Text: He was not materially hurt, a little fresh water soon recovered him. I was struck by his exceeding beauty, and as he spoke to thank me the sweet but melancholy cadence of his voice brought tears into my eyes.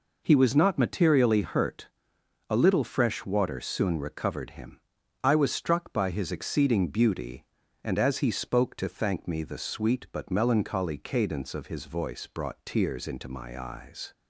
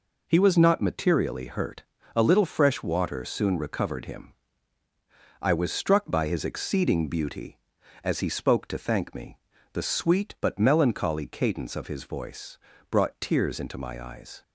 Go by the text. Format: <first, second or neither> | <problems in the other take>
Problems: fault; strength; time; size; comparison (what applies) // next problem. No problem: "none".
first | skips "and"; at 7.8 s // pauses between "me" and "the"; slight; at 9.3 s; 0.36 s long // pauses between "voice" and "brought"; slight; at 12.5 s; 0.34 s long